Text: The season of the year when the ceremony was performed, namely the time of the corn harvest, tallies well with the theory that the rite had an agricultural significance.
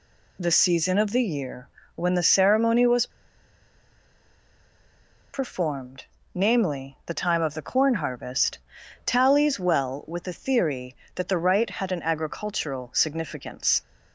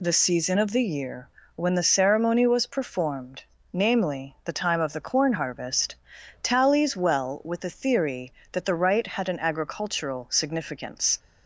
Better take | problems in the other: second | pauses between "year" and "when"; slight; at 1.6 s; 0.28 s long; slight in the second // pauses between "was" and "performed"; strong; at 3.0 s; 2.2 s long

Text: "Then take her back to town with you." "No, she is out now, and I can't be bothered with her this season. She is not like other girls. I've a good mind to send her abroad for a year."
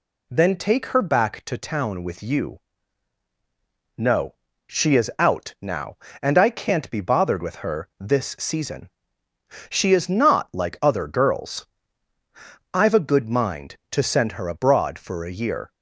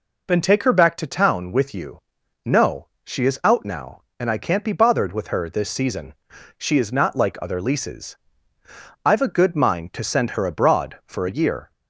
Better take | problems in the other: first | says "leases" for "girls"; at 7.6 s

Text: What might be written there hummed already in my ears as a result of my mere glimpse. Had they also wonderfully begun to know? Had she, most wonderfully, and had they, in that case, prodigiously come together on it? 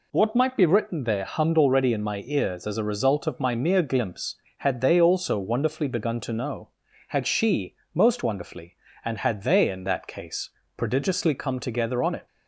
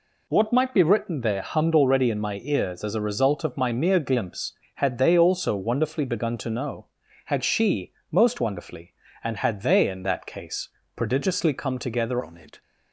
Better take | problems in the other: first | changes voice at "on"; from 12.2 s on; 0.4 s long

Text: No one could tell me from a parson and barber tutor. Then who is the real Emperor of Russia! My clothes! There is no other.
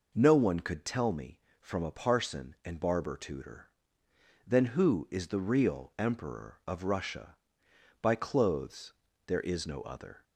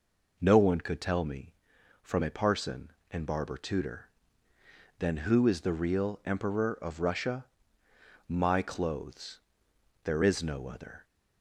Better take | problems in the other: second | says "By" for "My"; at 8.0 s

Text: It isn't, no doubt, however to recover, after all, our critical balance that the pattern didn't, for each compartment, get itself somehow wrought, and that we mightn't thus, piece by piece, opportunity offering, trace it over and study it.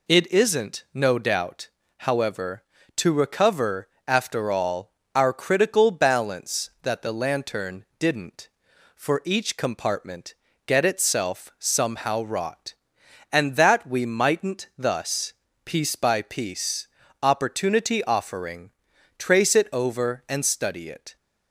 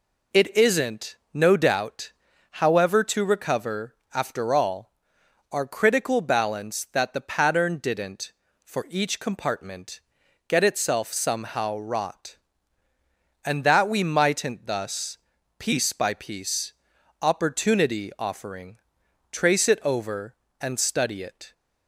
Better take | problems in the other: second | says "lantern" for "pattern"; at 7.1 s

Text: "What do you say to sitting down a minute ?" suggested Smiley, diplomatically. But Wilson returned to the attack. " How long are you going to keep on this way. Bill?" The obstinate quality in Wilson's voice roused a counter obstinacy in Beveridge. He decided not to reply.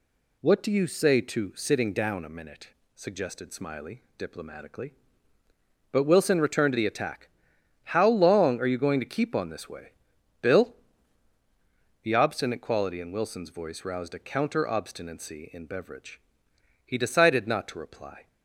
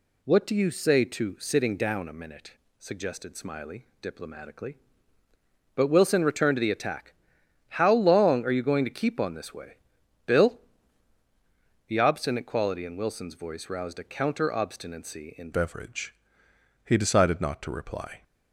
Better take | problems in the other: first | changes voice at "Beveridge"; from 15.5 s on; 2.7 s long

